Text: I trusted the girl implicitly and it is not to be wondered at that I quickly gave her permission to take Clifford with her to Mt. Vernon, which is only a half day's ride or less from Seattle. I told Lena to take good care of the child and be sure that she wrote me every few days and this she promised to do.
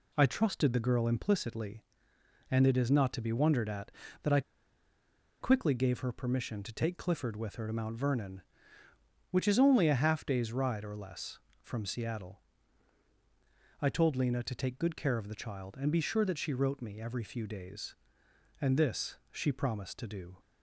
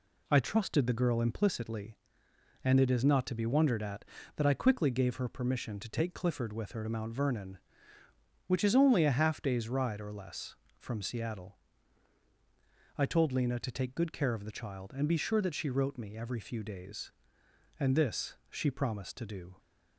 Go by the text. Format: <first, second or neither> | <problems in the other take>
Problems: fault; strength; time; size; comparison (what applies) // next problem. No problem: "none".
second | pauses between "I" and "quickly"; at 4.4 s; 1.0 s long